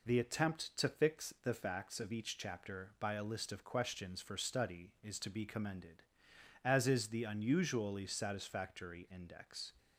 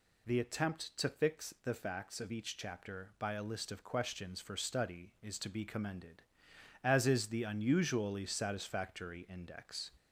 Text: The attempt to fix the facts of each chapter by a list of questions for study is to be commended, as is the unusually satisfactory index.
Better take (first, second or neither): first